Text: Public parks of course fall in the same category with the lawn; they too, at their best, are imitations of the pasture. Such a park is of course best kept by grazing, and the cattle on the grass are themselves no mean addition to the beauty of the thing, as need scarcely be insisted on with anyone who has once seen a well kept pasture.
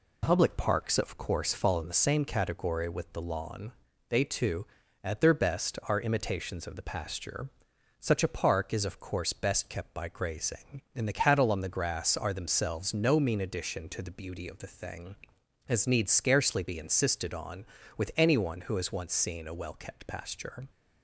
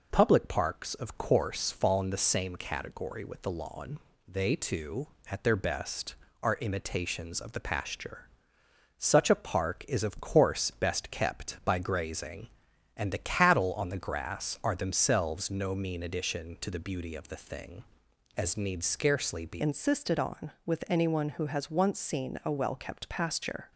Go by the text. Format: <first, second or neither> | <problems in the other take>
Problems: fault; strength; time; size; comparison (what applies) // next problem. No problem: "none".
first | changes voice at "insisted"; from 19.6 s on; 4.1 s long